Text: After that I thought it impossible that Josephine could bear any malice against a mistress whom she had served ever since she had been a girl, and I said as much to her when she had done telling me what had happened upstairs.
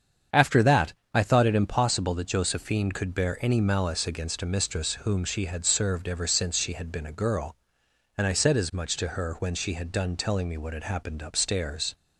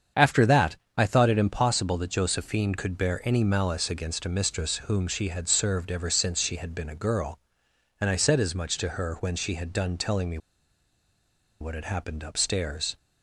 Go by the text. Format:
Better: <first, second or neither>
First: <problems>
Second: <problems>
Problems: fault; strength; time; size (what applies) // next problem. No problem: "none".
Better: first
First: starts louder than the rest; strong; until 1.5 s; 7.5 dB // pauses between "that" and "I"; slight; at 0.9 s; 0.22 s long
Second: starts louder than the rest; strong; until 1.3 s; 7.5 dB // pauses between "that" and "I"; slight; at 0.7 s; 0.22 s long // pauses between "me" and "what"; at 10.3 s; 1.2 s long